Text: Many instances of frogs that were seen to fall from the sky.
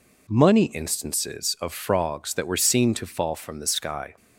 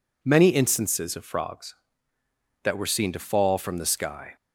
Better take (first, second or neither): second